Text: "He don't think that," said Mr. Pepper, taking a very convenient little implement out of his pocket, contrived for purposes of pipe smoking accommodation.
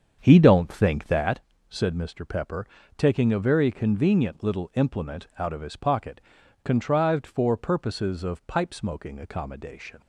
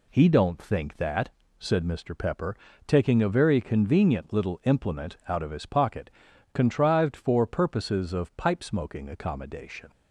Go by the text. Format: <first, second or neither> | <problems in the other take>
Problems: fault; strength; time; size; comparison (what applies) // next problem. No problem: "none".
second | starts louder than the rest; strong; until 1.3 s; 7.5 dB